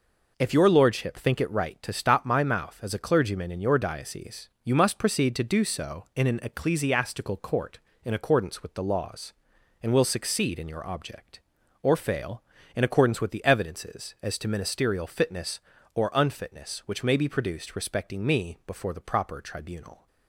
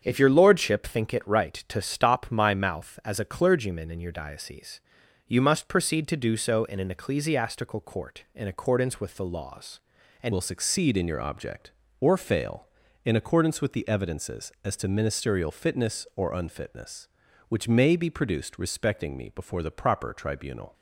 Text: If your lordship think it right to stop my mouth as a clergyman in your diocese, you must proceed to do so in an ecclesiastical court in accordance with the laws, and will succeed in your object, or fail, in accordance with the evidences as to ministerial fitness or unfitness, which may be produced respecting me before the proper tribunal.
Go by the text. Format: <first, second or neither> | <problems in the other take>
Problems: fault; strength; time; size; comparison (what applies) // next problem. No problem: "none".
first | starts louder than the rest; strong; until 1.0 s; 7.5 dB // changes voice at "will"; from 10.3 s on; 10.4 s long